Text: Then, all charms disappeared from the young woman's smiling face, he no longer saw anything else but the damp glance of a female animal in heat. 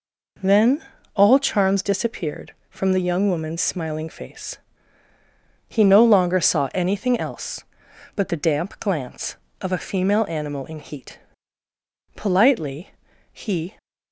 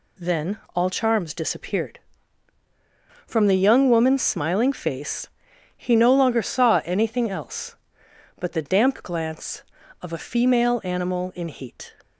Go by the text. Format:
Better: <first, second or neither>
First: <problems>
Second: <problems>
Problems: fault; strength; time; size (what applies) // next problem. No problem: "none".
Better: second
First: goes on to say "Politely he"; from 12.1 s on; 1.6 s long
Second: none